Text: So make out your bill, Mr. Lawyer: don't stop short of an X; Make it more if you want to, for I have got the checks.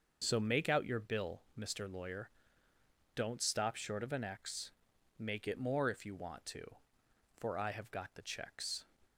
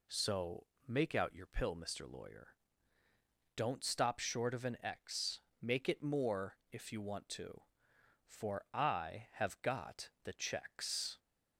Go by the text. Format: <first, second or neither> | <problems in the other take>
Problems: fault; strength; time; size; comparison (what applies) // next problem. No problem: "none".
first | pauses between "So" and "make"; slight; at 0.6 s; 0.24 s long // says "pill" for "bill"; at 1.4 s // pauses between "more" and "if"; slight; at 6.5 s; 0.16 s long